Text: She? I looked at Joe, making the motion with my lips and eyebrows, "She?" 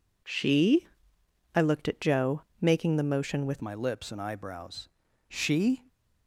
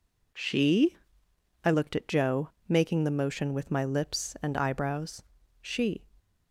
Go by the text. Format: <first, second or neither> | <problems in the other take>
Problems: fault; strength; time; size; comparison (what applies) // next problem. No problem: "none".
second | changes voice at "my"; from 3.6 s on; 2.2 s long